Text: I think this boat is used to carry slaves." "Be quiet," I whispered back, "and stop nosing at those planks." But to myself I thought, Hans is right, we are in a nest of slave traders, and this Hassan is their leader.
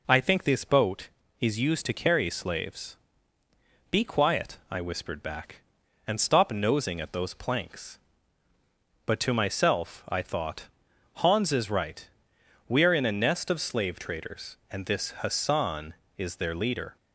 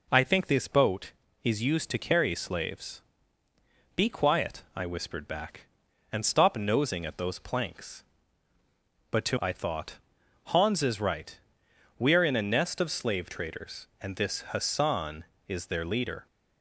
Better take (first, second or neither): first